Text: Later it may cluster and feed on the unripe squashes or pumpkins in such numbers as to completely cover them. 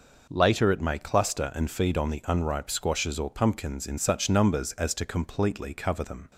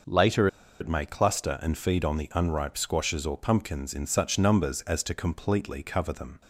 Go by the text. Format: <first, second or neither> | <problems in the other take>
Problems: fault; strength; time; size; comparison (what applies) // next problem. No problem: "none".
first | pauses between "Later" and "it"; slight; at 0.4 s; 0.32 s long